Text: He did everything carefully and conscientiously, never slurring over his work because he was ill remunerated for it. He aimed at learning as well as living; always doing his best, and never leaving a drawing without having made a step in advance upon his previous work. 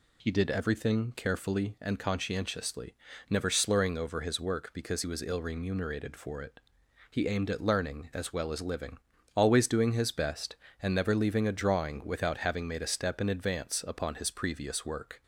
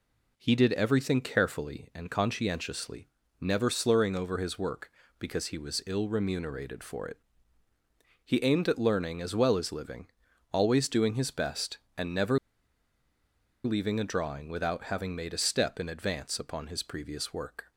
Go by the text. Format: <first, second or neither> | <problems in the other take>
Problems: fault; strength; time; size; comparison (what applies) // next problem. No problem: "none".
first | pauses between "never" and "leaving"; strong; at 12.3 s; 1.2 s long